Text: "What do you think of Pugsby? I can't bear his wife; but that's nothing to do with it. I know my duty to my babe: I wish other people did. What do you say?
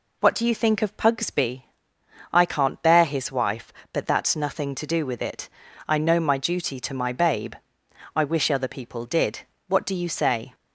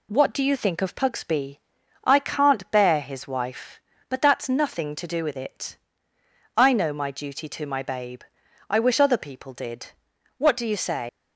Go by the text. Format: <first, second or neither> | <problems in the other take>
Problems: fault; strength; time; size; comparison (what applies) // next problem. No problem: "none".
first | leaves "say" unfinished; at 11.0 s; 125 ms